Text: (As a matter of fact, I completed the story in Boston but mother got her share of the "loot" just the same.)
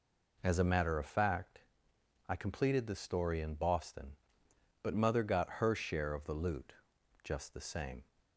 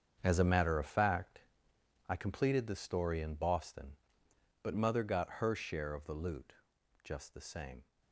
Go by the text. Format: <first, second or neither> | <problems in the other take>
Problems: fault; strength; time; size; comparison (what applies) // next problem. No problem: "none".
first | gets quieter; strong; throughout; 11.5 dB // pauses between "loot" and "just"; noticeable; at 6.5 s; 0.50 s long; noticeable in the first